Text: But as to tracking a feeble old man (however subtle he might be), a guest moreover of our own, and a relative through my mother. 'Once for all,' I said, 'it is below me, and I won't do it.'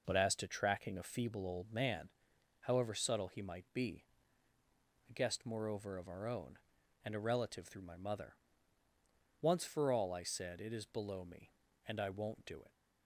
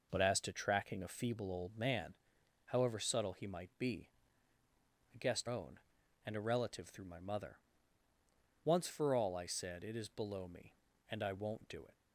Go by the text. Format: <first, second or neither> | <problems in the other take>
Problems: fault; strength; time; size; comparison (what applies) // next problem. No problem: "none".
first | skips "moreover of our"; at 5.4 s